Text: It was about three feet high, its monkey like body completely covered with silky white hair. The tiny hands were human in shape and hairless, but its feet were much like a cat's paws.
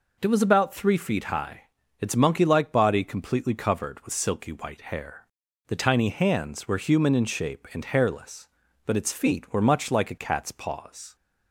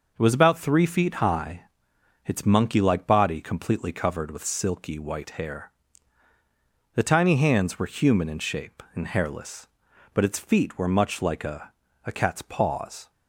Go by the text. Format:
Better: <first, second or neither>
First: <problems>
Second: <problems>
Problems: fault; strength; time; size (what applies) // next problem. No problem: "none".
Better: first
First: none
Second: says "a" twice; at 12.0 s